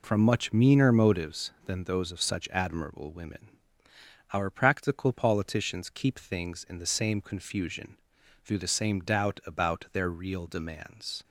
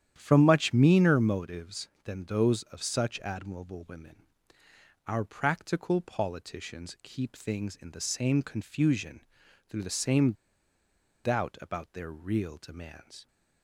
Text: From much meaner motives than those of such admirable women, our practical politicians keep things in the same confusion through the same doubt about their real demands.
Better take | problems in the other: first | starts louder than the rest; strong; until 1.1 s; 10 dB // pauses between "confusion" and "through"; noticeable; at 9.2 s; 0.48 s long; noticeable in the first // pauses between "same" and "doubt"; noticeable; at 10.3 s; 0.91 s long

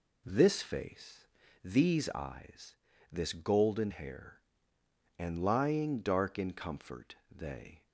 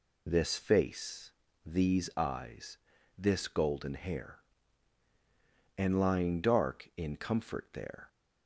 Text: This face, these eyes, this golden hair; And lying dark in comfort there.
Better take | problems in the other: second | says "they" for "there"; at 7.2 s

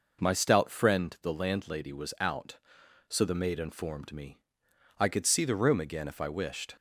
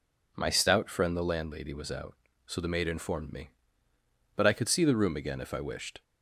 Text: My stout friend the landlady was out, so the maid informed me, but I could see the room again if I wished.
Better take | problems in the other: second | skips "but"; at 4.6 s

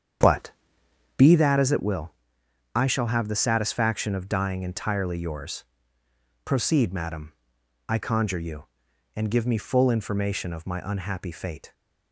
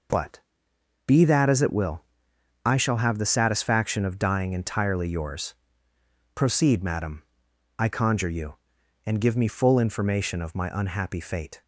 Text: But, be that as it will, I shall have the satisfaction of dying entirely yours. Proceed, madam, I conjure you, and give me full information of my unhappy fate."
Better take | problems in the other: second | starts louder than the rest; strong; until 1.4 s; 8 dB

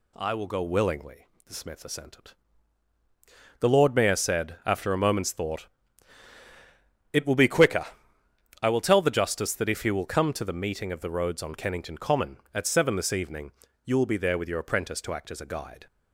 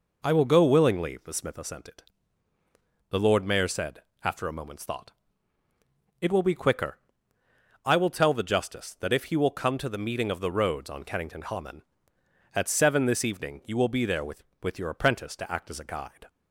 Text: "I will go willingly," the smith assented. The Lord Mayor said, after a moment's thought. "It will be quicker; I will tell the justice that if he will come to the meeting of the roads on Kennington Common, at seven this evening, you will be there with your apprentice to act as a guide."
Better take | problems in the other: first | says "with" twice; at 14.6 s

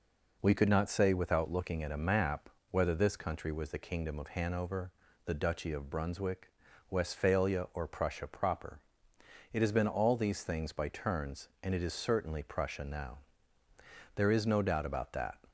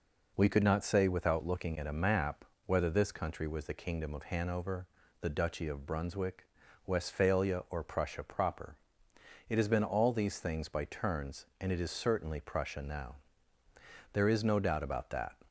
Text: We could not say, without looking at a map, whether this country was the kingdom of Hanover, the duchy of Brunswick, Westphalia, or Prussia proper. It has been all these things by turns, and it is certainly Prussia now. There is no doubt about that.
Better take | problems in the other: neither | none

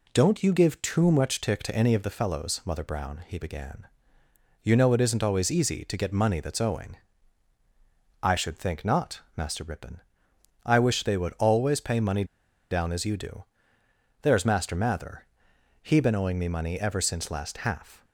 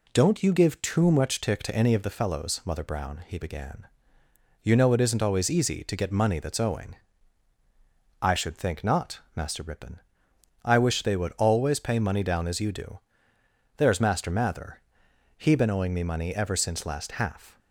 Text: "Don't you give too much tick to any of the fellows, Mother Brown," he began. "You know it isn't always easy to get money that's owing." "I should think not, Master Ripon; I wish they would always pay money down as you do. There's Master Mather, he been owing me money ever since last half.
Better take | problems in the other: second | pauses between "money" and "down"; noticeable; at 12.2 s; 0.46 s long

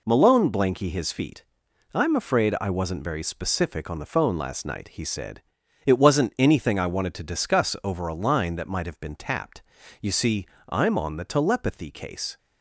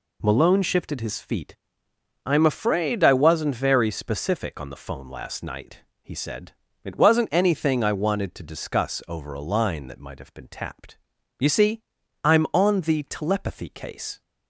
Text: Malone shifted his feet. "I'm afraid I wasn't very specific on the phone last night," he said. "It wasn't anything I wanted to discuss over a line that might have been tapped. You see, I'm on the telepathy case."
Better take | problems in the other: second | says "blanky" for "shifted"; at 0.4 s

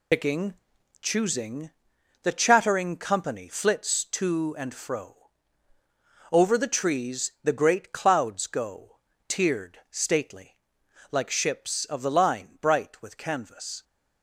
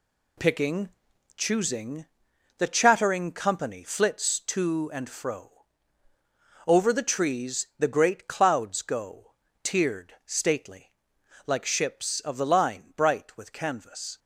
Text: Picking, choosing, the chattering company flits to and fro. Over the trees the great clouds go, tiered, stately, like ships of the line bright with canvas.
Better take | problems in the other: second | loses the start of "Picking"; at 0.1 s; 95 ms

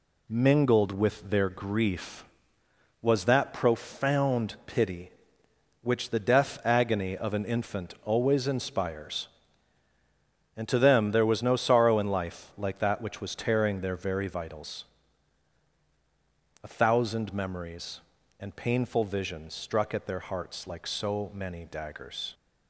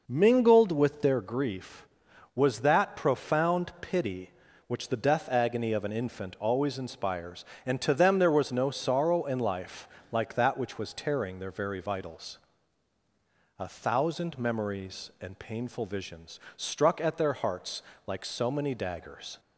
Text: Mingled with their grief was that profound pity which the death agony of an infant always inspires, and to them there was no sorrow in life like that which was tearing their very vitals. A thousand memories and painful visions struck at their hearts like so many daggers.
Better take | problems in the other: first | starts louder than the rest; noticeable; until 1.2 s; 5.5 dB // pauses between "life" and "like"; slight; at 9.8 s; 0.24 s long // pauses between "visions" and "struck"; slight; at 16.3 s; 0.16 s long // pauses between "hearts" and "like"; slight; at 17.8 s; 0.24 s long

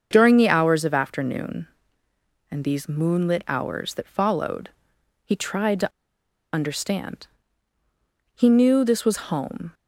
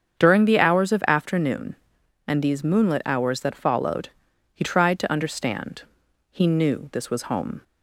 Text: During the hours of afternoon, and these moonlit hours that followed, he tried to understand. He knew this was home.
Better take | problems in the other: second | starts louder than the rest; until 1.1 s; 7 dB; strong in the second // pauses between "to" and "understand"; noticeable; at 5.9 s; 0.64 s long

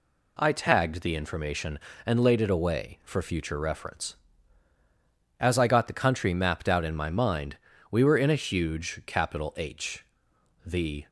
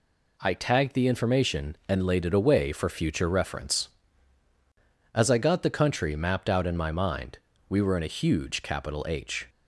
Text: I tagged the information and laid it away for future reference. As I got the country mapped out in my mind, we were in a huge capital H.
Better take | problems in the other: second | goes on to say "The"; slight; from 10.6 s on; 0.42 s long

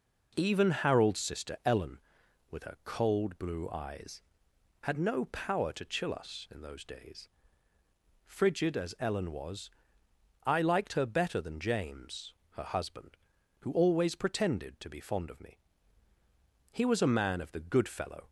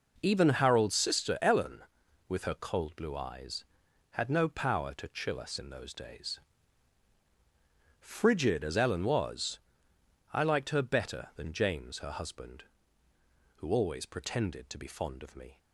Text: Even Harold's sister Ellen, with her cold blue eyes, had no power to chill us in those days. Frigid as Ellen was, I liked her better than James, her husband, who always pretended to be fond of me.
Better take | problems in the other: second | goes on to say "He was a man of the good fellow"; from 16.7 s on; 1.5 s long

